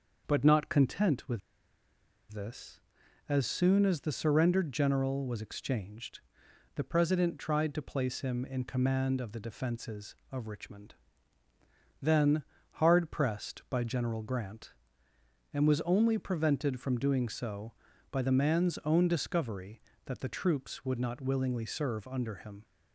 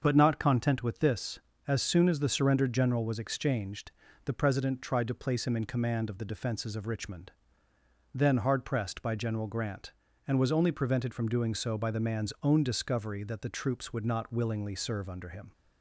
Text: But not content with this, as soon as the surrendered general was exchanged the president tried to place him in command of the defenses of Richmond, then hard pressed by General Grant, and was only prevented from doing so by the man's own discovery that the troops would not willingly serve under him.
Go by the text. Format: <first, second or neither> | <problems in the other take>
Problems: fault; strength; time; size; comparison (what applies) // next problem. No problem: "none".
second | starts louder than the rest; until 1.2 s; 6 dB; also in the second // pauses between "with" and "this"; noticeable; at 1.4 s; 0.91 s long // pauses between "exchanged" and "the"; noticeable; at 6.1 s; 0.56 s long; slight in the second // pauses between "then" and "hard"; slight; at 12.4 s; 0.30 s long